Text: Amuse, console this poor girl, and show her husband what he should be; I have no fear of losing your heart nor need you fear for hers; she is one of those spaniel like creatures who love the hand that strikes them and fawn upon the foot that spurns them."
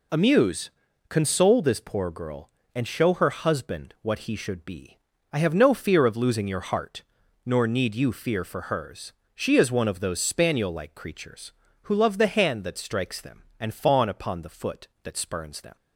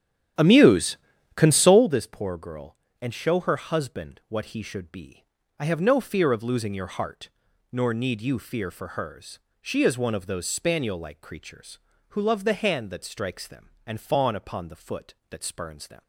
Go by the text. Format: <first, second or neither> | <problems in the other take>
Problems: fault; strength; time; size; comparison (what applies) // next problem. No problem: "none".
first | starts louder than the rest; strong; until 2.0 s; 10.5 dB // pauses between "heart" and "nor"; at 7.2 s; 0.42 s long; also in the first